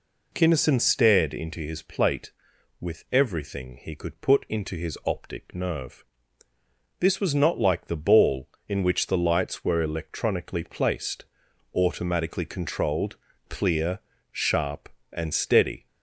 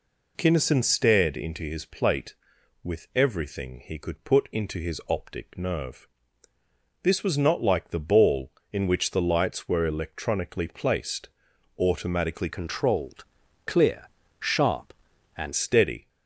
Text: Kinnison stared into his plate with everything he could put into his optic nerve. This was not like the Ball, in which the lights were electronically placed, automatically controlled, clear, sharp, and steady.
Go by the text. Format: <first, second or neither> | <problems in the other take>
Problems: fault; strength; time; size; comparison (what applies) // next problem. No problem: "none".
first | changes voice from "controlled" to "and"; from 12.5 to 15.5 s; 3.0 s long